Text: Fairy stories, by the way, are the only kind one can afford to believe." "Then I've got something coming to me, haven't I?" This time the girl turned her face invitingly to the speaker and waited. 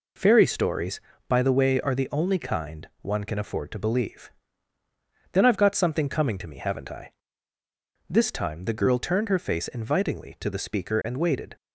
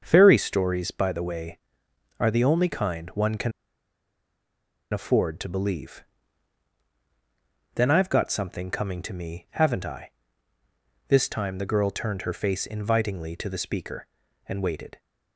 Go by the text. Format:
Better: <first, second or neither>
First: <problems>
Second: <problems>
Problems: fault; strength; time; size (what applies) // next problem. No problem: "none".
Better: first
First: none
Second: starts louder than the rest; until 1.0 s; 6.5 dB // pauses between "can" and "afford"; strong; at 3.5 s; 1.4 s long